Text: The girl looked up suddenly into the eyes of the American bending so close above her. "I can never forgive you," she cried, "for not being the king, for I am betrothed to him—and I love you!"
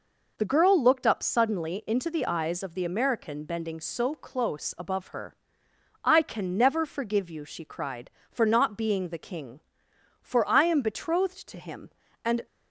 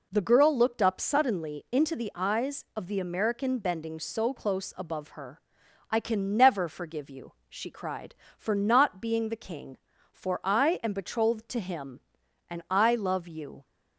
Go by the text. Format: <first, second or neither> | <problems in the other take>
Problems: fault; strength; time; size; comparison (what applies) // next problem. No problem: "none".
second | stops before "I love you"; at 12.4 s